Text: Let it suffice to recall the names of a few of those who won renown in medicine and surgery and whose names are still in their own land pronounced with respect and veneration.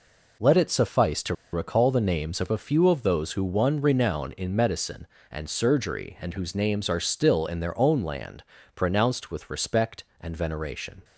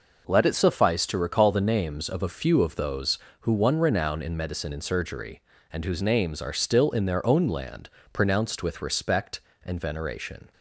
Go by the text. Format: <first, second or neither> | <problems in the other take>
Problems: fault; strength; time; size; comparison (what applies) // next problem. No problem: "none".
second | pauses between "to" and "recall"; slight; at 1.3 s; 0.18 s long // pauses between "land" and "pronounced"; slight; at 8.4 s; 0.30 s long; slight in the second